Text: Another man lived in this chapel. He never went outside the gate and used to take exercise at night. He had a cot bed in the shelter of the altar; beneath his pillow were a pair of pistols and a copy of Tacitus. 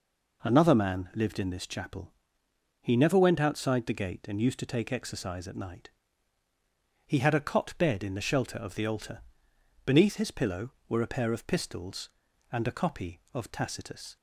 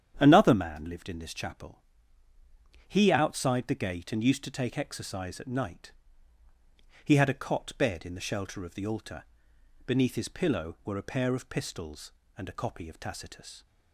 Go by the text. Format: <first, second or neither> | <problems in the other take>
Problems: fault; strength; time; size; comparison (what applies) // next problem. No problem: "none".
first | starts louder than the rest; strong; until 1.1 s; 9 dB // skips "never went"; at 3.1 s